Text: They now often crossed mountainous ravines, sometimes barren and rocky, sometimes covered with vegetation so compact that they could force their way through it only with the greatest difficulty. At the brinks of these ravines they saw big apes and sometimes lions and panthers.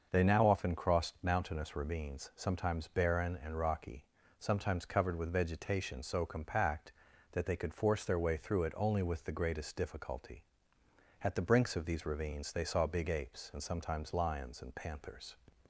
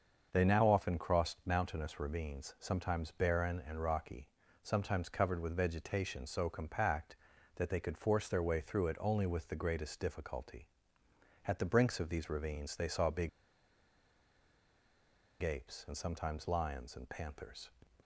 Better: first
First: starts louder than the rest; until 1.1 s; 6 dB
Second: starts louder than the rest; until 1.3 s; 6.5 dB // pauses between "big" and "apes"; strong; at 13.2 s; 2.1 s long

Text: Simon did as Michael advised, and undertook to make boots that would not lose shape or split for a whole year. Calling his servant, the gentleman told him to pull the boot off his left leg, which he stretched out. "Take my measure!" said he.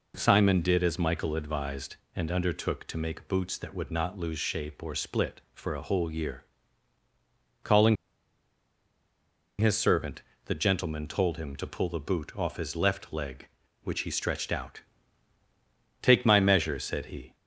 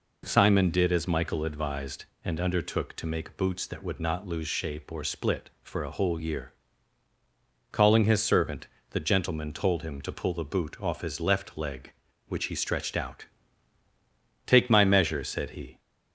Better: second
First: pauses between "Calling" and "his"; strong; at 7.9 s; 1.6 s long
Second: none

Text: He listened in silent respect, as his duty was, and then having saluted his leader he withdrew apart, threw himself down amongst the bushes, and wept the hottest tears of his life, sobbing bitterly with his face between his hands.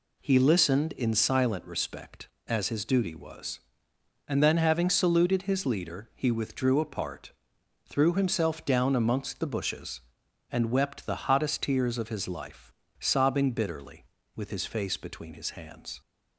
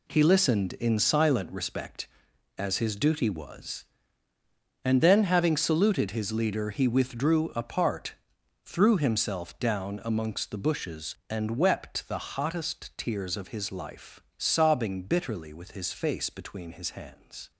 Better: first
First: none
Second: gets quieter; strong; throughout; 10 dB

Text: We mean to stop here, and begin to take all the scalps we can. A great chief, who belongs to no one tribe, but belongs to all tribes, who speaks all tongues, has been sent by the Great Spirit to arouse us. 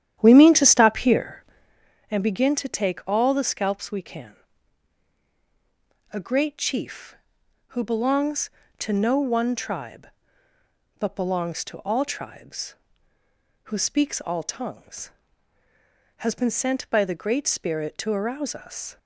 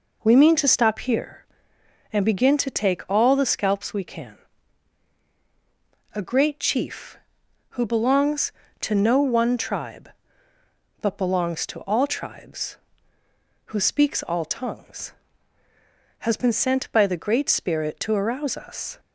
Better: second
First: starts louder than the rest; strong; until 1.9 s; 10.5 dB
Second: none

